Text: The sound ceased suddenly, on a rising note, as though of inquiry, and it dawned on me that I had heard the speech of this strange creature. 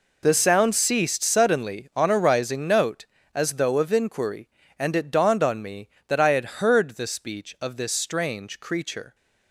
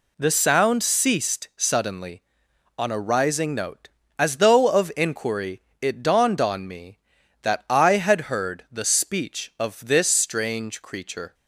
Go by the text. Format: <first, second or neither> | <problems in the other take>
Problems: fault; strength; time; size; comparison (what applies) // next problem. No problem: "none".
first | skips "and"; at 5.7 s